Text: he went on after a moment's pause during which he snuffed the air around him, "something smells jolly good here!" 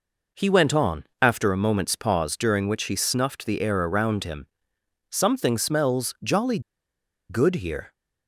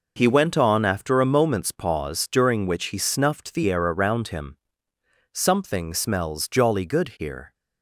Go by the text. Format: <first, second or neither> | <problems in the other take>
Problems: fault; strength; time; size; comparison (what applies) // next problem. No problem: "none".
second | pauses between "on" and "after"; slight; at 1.0 s; 0.16 s long // pauses between "jolly" and "good"; noticeable; at 6.5 s; 0.70 s long